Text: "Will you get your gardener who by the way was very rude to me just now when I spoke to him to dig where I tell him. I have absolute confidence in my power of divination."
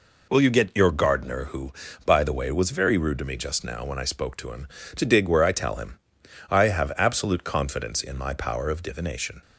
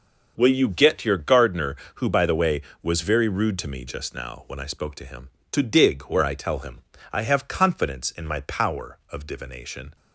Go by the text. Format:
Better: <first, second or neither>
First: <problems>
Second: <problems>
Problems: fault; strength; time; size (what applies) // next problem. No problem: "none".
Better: first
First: none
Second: skips "absolute"; at 7.4 s